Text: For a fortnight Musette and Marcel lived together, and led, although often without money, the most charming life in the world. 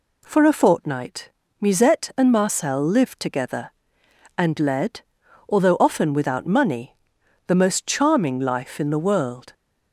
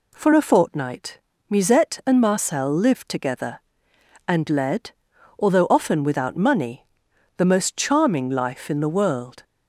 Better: neither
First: pauses between "fortnight" and "Musette"; slight; at 1.3 s; 0.30 s long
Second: pauses between "fortnight" and "Musette"; slight; at 1.1 s; 0.30 s long

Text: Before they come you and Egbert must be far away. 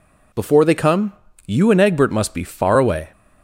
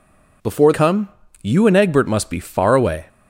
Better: first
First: pauses between "come" and "you"; slight; at 1.1 s; 0.32 s long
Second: skips "they"; at 0.7 s // pauses between "come" and "you"; slight; at 1.0 s; 0.32 s long

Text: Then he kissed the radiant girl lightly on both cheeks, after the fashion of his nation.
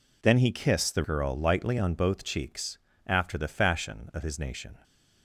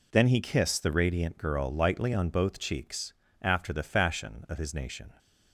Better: second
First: skips "radiant"; at 1.0 s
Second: none

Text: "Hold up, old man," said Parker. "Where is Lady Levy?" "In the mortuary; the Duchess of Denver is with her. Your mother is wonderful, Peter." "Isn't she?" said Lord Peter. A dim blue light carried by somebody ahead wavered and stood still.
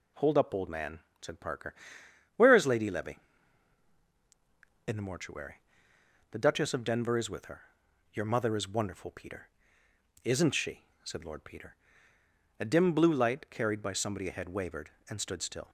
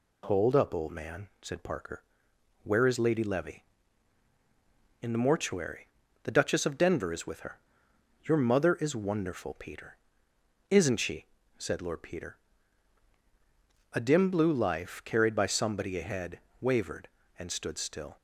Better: first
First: none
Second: says "life" for "light"; at 14.5 s // pauses between "ahead" and "wavered"; slight; at 16.4 s; 0.18 s long

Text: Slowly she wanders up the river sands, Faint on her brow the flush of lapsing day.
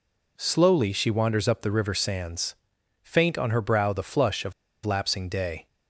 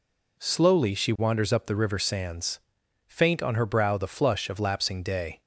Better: second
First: pauses between "of" and "lapsing"; slight; at 4.5 s; 0.32 s long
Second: none

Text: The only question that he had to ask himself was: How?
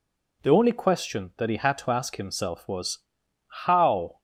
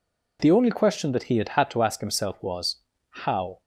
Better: first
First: none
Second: says "had" twice; at 1.4 s

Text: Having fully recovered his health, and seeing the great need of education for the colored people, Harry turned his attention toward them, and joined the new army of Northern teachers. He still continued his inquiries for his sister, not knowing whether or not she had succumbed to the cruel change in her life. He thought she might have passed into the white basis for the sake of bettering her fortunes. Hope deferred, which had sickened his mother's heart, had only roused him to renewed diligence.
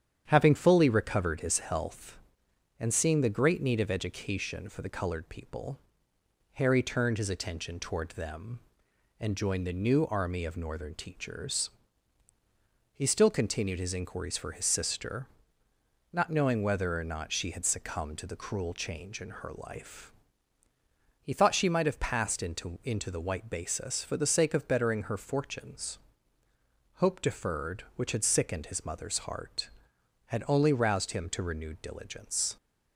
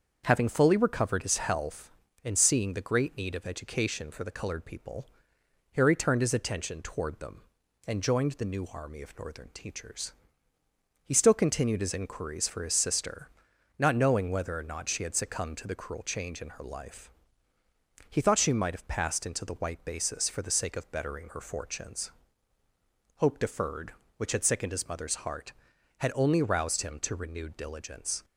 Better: second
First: starts louder than the rest; strong; until 1.3 s; 9 dB // says "into" twice; at 22.8 s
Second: starts louder than the rest; until 1.2 s; 6.5 dB

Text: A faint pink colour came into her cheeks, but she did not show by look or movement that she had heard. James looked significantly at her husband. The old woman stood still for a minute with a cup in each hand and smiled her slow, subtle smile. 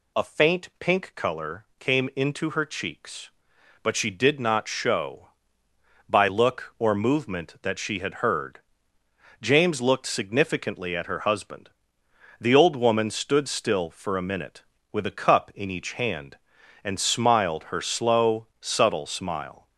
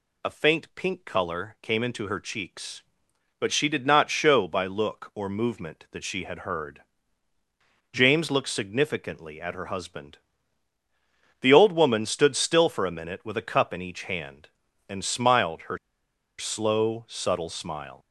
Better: first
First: none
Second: pauses between "her" and "slow"; noticeable; at 15.7 s; 0.61 s long

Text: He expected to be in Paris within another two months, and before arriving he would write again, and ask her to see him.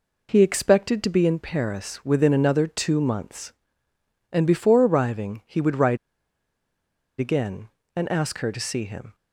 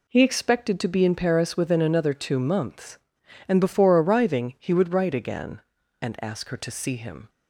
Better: second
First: pauses between "write" and "again"; at 5.9 s; 1.2 s long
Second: none

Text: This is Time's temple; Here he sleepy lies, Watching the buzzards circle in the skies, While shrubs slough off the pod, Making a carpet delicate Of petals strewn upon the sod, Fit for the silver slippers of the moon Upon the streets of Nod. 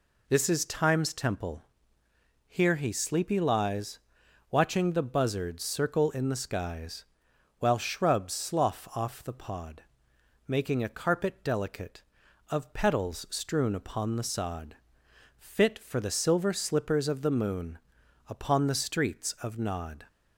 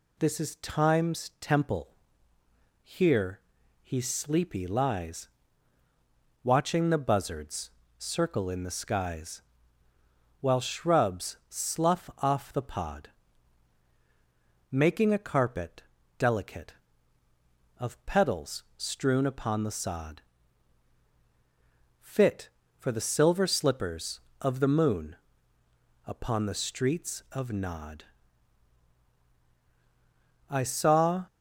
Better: first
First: pauses between "moon" and "Upon"; noticeable; at 17.7 s; 0.50 s long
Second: pauses between "Here" and "he"; at 3.3 s; 0.44 s long // pauses between "buzzards" and "circle"; slight; at 7.6 s; 0.30 s long // pauses between "carpet" and "delicate"; slight; at 15.8 s; 0.34 s long // pauses between "moon" and "Upon"; noticeable; at 25.1 s; 0.92 s long // goes on to say "I saw"; noticeable; from 30.4 s on; 0.76 s long

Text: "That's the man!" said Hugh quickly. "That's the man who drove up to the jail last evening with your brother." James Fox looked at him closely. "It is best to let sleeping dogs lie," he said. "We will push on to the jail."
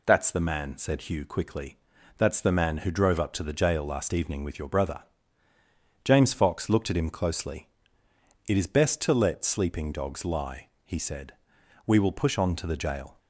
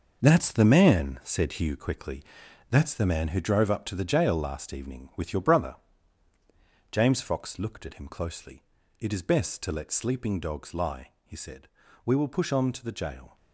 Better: first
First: none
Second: gets quieter; strong; throughout; 9 dB

